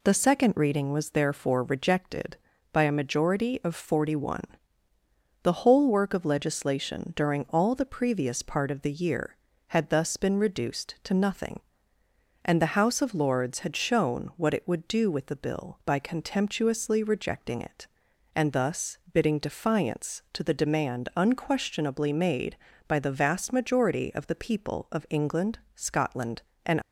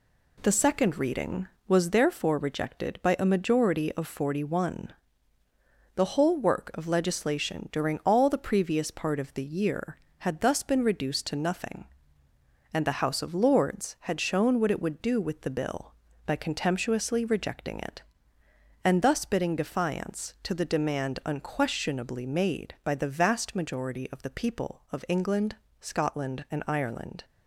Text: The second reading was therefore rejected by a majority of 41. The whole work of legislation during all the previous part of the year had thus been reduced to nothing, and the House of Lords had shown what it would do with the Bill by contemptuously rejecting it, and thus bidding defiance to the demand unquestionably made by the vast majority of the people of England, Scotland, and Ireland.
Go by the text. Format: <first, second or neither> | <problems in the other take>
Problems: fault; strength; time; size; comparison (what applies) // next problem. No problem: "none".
second | pauses between "thus" and "bidding"; slight; at 18.9 s; 0.16 s long // stops before "Ireland"; at 26.8 s